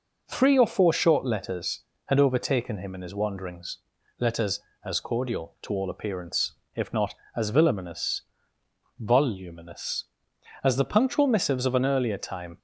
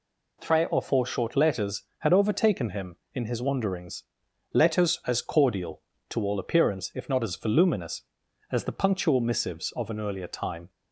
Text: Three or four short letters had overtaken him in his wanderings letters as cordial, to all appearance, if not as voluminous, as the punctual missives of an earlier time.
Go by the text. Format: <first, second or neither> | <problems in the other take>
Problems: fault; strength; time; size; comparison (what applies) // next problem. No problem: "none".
second | pauses between "wanderings" and "letters"; at 3.7 s; 0.40 s long; noticeable in the second // says "voluminous" twice; at 8.9 s